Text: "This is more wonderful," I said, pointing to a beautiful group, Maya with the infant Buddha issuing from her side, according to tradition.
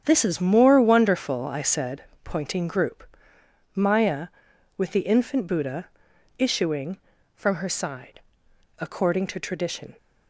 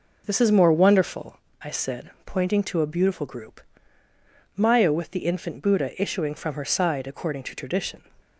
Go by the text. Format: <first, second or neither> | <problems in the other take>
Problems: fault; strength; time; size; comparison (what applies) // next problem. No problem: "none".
second | starts louder than the rest; strong; until 1.0 s; 8 dB // skips "to a beautiful"; at 2.6 s // pauses between "Buddha" and "issuing"; noticeable; at 5.8 s; 0.50 s long